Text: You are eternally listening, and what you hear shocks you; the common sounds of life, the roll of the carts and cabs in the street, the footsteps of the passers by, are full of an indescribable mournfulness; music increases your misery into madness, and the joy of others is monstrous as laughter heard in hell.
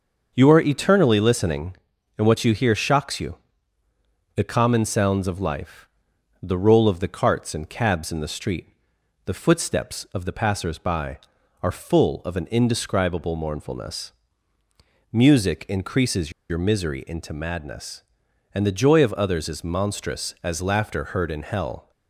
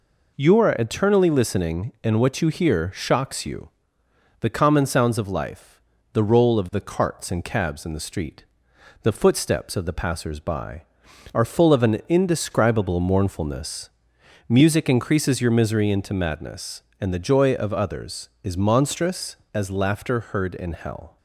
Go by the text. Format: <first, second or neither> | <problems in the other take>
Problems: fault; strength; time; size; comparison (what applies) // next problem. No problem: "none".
second | starts louder than the rest; until 1.3 s; 6.5 dB // pauses between "increases" and "your"; slight; at 16.3 s; 0.18 s long